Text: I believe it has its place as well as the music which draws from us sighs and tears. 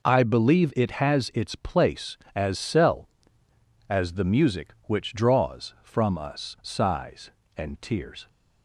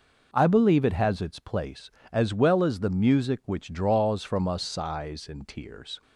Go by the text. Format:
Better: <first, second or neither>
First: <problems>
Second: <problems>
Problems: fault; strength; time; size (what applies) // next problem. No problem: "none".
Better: second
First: says "cell" for "well"; at 2.5 s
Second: none